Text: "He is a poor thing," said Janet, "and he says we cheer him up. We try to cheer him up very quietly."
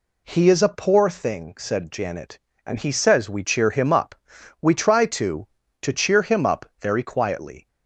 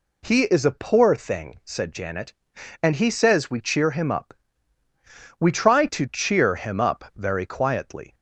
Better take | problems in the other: second | says "to" twice; at 5.8 s // pauses between "up" and "very"; slight; at 6.6 s; 0.16 s long

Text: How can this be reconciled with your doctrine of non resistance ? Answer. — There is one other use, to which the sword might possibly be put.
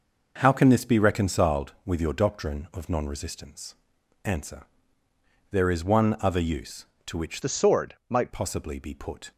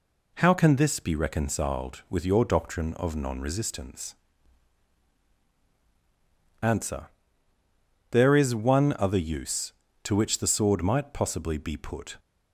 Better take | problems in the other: second | changes voice from "the" to "might"; from 7.4 to 8.3 s; 0.9 s long

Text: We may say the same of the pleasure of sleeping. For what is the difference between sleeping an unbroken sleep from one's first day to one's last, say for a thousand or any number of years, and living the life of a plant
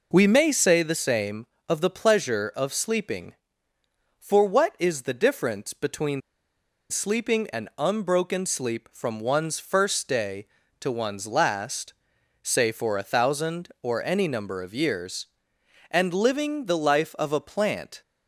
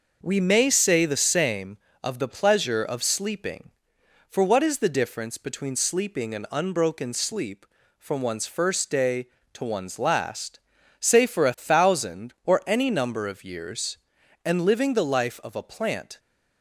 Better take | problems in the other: second | pauses between "between" and "sleeping"; noticeable; at 6.1 s; 0.70 s long

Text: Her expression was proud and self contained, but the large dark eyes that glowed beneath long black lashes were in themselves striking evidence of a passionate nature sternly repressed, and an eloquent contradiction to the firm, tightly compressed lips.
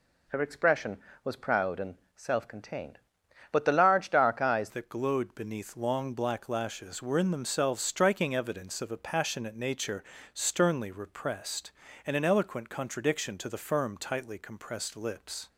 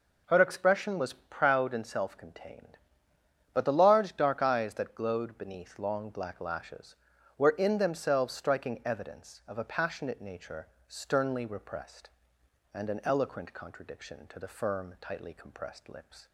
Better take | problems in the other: second | pauses between "and" and "self"; slight; at 1.9 s; 0.20 s long // changes voice at "that"; from 4.6 s on; 10.8 s long // pauses between "nature" and "sternly"; slight; at 10.0 s; 0.30 s long; slight in the second

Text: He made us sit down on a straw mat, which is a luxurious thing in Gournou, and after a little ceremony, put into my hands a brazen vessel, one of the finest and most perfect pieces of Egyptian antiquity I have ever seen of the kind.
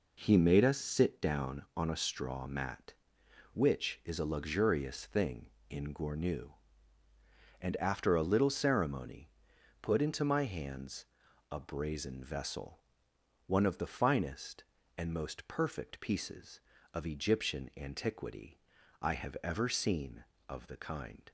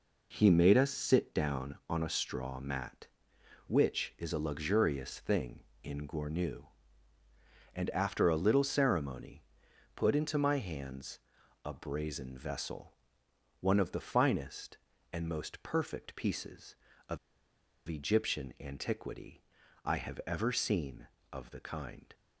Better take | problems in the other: first | pauses between "hands" and "a"; noticeable; at 11.1 s; 0.46 s long; noticeable in the first // pauses between "of" and "Egyptian"; noticeable; at 17.1 s; 0.69 s long // pauses between "antiquity" and "I"; at 19.4 s; 0.44 s long; also in the first

